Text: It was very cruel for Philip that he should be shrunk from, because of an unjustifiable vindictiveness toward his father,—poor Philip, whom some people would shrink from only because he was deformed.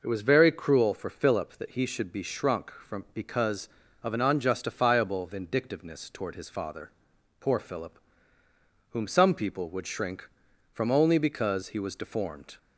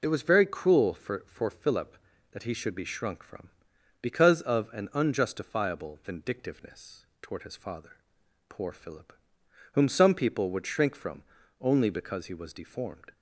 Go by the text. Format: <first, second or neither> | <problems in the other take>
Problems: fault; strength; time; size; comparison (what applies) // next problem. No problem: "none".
first | says "for" twice; at 1.2 s // pauses between "vindictiveness" and "toward"; slight; at 7.0 s; 0.16 s long // pauses between "from" and "only"; at 11.2 s; 0.38 s long